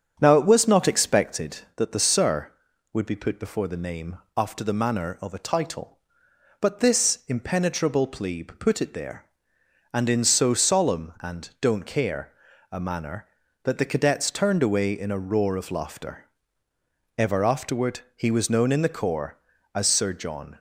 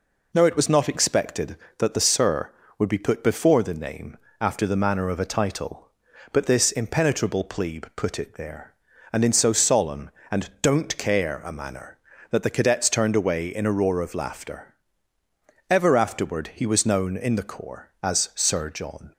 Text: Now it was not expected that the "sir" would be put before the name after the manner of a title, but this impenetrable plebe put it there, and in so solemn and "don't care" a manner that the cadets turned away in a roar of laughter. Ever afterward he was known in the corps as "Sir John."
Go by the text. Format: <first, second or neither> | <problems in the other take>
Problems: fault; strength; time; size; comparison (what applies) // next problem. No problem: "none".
second | starts louder than the rest; strong; until 1.5 s; 7.5 dB // pauses between "name" and "after"; slight; at 4.1 s; 0.18 s long; slight in the second // pauses between "care" and "a"; at 12.3 s; 0.40 s long // pauses between "afterward" and "he"; slight; at 18.0 s; 0.16 s long